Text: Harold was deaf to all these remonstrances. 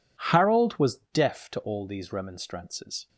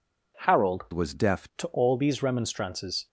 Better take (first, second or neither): first